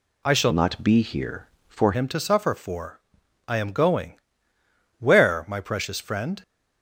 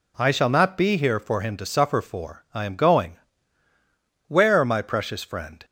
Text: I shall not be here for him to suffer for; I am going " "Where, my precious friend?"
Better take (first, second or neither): second